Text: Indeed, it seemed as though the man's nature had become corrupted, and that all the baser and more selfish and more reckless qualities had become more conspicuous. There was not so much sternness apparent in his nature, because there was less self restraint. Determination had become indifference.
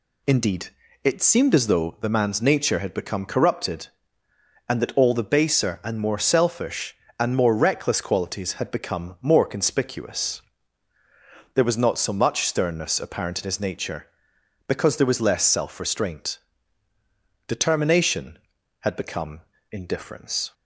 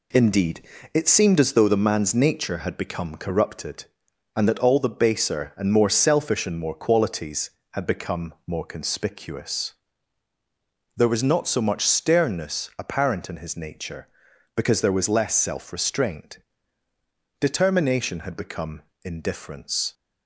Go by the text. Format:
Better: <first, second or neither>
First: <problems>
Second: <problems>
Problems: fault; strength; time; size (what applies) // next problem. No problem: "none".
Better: first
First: pauses between "become" and "indifference"; slight; at 19.4 s; 0.30 s long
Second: skips "reckless"; at 6.7 s // pauses between "become" and "indifference"; slight; at 18.8 s; 0.22 s long